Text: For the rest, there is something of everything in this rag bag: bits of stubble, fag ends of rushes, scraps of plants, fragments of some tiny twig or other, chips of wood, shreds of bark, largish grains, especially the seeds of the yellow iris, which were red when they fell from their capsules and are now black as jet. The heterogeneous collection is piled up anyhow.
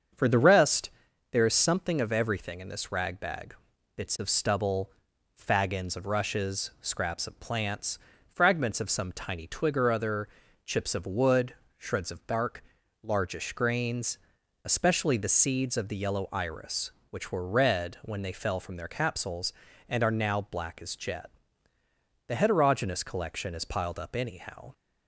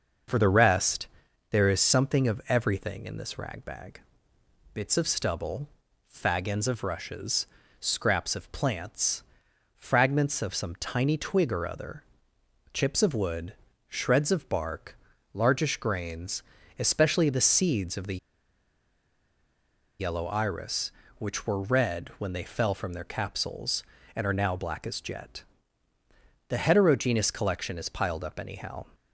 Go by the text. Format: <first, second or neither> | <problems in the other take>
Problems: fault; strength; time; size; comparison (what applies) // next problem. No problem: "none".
first | starts louder than the rest; until 1.7 s; 6 dB; also in the first // pauses between "the" and "yellow"; strong; at 18.1 s; 1.8 s long